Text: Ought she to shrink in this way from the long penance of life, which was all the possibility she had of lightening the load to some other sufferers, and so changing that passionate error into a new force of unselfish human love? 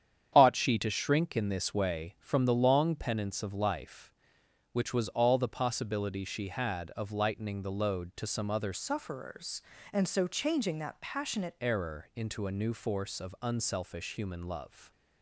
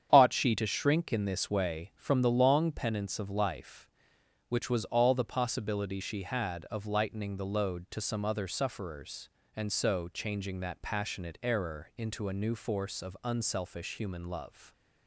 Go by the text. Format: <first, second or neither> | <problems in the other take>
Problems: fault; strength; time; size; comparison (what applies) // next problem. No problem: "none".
second | starts louder than the rest; strong; until 1.3 s; 8.5 dB; strong in the second // changes voice from "sufferers" to "passionate"; from 8.7 to 11.5 s; 2.8 s long